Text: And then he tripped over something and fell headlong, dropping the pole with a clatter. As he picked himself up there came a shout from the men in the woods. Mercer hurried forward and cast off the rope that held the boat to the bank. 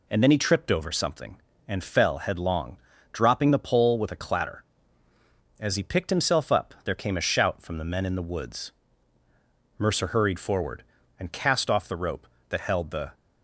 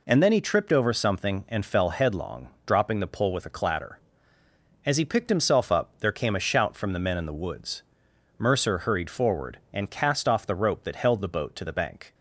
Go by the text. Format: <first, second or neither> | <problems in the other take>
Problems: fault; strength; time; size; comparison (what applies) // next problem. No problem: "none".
second | stops before "boat to the bank"; at 13.1 s